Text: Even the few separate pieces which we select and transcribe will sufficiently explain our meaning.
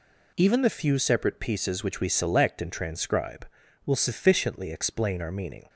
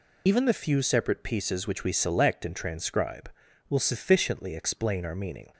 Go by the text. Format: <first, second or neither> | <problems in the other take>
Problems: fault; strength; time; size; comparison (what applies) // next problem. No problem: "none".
first | loses the start of "Even"; at 0.2 s; 70 ms